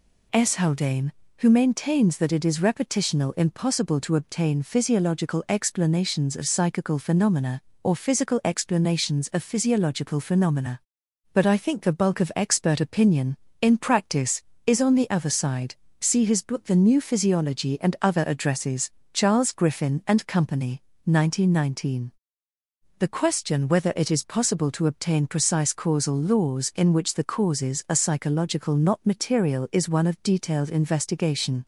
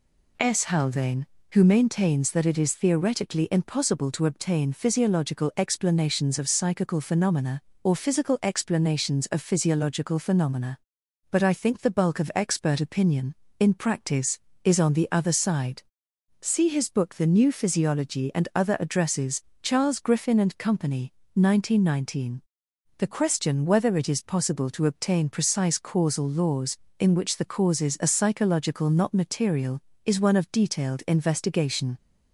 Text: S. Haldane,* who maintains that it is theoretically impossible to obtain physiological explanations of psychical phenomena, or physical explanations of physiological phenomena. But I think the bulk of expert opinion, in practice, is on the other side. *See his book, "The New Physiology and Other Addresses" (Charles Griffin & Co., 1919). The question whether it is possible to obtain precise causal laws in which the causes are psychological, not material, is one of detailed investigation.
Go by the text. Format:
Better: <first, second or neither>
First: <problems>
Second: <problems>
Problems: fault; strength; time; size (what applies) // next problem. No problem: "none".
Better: second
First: says "repetitional" for "theoretically"; at 2.5 s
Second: none